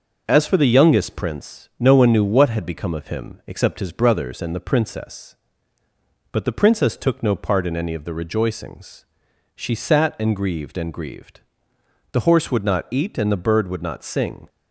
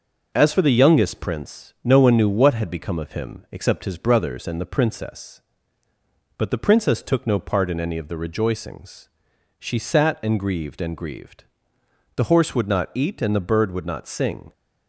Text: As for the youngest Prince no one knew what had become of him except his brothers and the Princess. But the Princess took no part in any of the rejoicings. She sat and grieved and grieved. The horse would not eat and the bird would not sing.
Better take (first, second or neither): neither